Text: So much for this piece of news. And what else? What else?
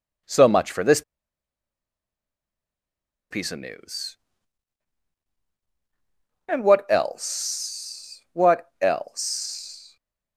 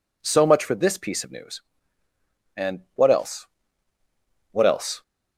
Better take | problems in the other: second | pauses between "this" and "piece"; strong; at 1.0 s; 2.2 s long

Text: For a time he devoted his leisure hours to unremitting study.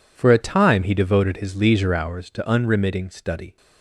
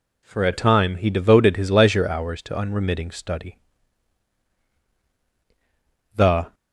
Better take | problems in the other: first | goes on to say "The"; slight; from 6.1 s on; 0.38 s long

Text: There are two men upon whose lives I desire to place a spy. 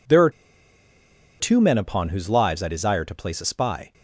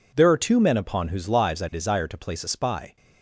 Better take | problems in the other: second | pauses between "are" and "two"; at 0.2 s; 1.1 s long

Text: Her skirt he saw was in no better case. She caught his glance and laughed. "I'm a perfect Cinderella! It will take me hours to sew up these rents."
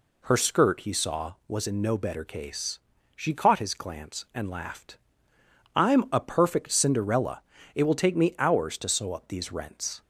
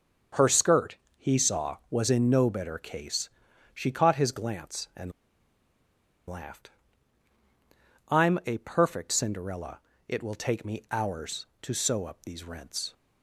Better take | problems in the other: first | starts louder than the rest; until 1.5 s; 6.5 dB // pauses between "skirt" and "he"; slight; at 0.9 s; 0.20 s long // pauses between "and" and "laughed"; at 5.1 s; 1.1 s long

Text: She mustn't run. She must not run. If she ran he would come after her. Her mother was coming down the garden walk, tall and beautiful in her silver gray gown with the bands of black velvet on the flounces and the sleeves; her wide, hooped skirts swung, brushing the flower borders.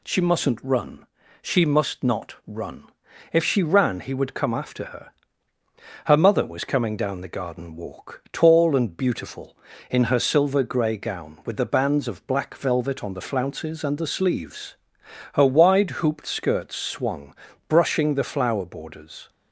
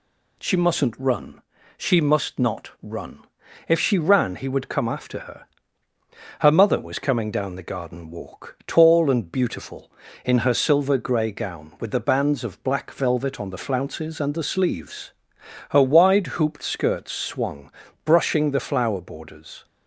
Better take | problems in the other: neither | none

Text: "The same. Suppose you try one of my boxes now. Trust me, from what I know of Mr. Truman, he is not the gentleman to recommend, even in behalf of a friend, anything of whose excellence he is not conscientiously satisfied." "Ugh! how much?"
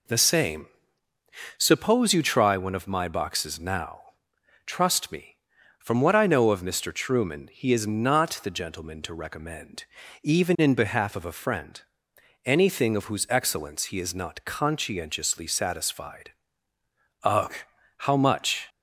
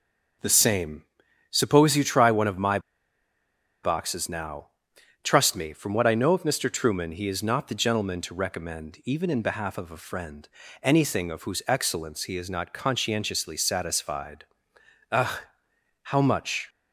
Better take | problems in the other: first | starts louder than the rest; noticeable; until 1.8 s; 6 dB // pauses between "my" and "boxes"; at 2.7 s; 1.0 s long

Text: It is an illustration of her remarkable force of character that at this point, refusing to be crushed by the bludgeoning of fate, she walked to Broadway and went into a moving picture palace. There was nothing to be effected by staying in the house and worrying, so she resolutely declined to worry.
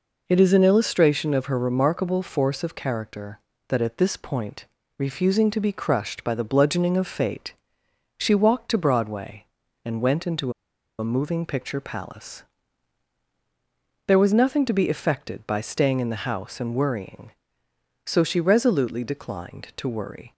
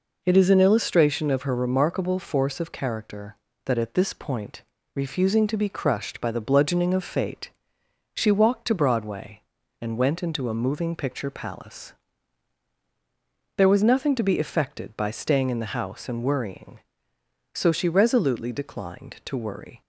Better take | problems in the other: second | pauses between "into" and "a"; noticeable; at 10.5 s; 0.46 s long

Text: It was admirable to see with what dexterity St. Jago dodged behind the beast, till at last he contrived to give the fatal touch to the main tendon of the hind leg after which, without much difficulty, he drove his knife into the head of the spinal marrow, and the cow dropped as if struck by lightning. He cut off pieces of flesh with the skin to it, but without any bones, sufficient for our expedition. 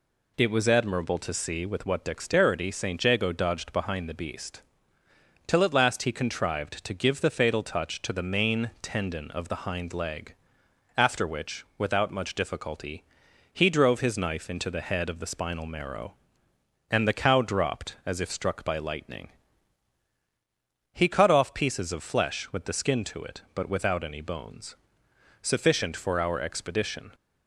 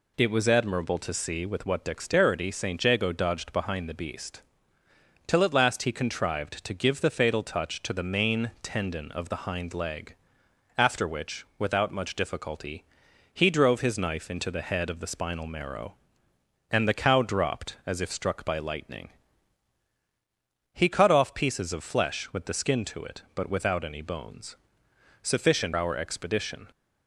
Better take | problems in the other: first | pauses between "leg" and "after"; noticeable; at 10.1 s; 0.60 s long; noticeable in the first // skips "for"; at 25.7 s

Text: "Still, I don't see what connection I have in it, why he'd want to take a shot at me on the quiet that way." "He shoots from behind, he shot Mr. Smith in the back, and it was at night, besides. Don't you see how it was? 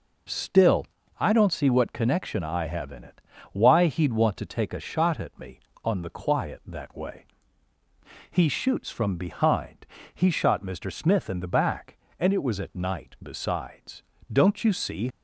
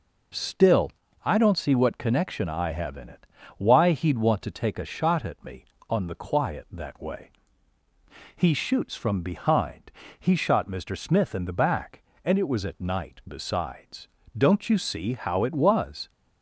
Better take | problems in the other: second | stops before "how it was"; at 15.1 s

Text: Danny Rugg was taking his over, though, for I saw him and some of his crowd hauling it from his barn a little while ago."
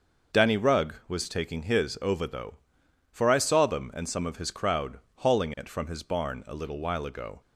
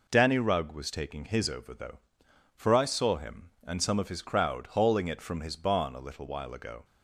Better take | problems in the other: second | says "them" for "him"; at 3.6 s // pauses between "crowd" and "hauling"; slight; at 4.9 s; 0.18 s long

